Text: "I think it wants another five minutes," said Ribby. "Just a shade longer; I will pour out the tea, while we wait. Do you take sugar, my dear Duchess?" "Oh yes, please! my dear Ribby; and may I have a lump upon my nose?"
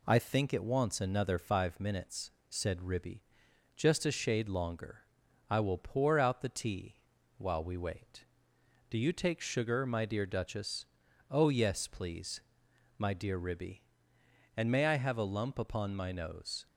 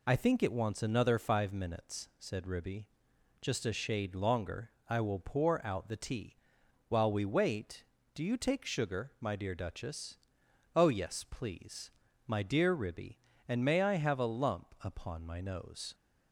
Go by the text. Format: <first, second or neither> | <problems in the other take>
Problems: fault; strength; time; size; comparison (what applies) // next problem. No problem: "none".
neither | none